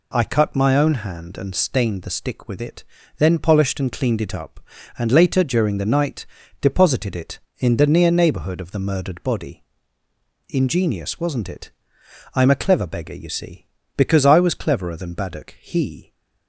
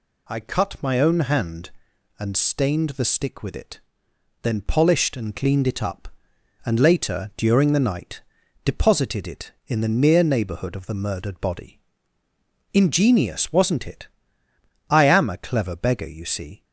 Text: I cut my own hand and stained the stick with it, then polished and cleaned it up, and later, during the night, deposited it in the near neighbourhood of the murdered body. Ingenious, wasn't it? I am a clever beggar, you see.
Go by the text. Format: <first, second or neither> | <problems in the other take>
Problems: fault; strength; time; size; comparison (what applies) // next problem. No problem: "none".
second | goes on to say "Because I was cleverer than Baddock he"; strong; from 13.9 s on; 2.1 s long